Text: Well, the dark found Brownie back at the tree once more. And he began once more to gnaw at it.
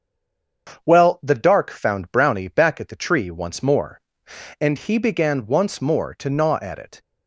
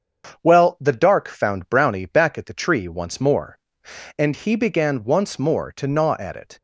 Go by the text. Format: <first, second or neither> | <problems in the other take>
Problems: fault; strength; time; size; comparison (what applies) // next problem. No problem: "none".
second | stays silent before the first word; slight; until 0.6 s; 0.6 s long // starts louder than the rest; until 1.8 s; 7 dB; also in the second